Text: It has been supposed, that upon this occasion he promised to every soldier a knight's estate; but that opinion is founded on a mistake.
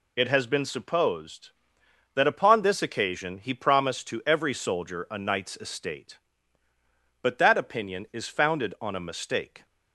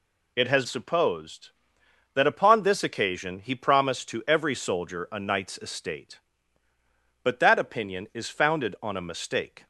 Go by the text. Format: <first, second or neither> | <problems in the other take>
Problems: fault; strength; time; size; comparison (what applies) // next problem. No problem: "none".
first | skips "been"; at 0.6 s